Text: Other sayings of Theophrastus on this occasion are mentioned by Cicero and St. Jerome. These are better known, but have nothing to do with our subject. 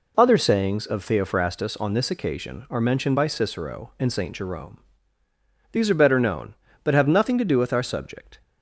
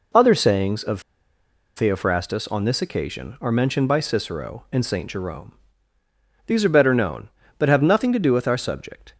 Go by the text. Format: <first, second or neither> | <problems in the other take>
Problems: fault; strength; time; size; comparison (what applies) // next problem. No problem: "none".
first | pauses between "of" and "Theophrastus"; noticeable; at 0.9 s; 0.76 s long